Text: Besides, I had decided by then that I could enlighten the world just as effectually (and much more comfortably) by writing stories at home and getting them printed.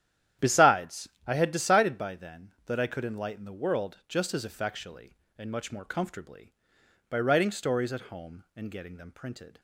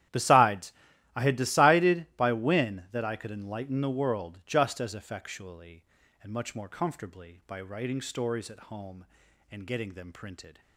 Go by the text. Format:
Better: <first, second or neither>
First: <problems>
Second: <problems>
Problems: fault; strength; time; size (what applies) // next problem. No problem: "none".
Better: first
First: starts louder than the rest; strong; until 1.5 s; 10.5 dB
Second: starts louder than the rest; strong; until 1.5 s; 11.5 dB // says "when" for "then"; at 2.3 s